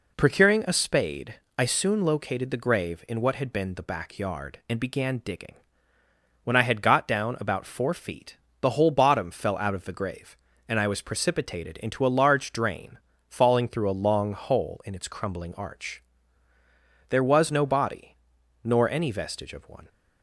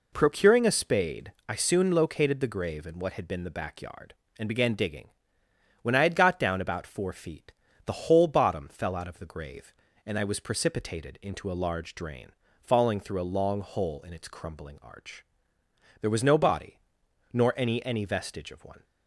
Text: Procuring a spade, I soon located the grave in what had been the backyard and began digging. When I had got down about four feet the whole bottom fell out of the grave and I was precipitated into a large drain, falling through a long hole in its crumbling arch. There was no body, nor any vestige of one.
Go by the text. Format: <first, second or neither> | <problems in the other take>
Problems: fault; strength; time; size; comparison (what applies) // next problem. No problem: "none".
first | pauses between "feet" and "the"; slight; at 7.5 s; 0.34 s long; slight in the first // says "any" twice; at 17.8 s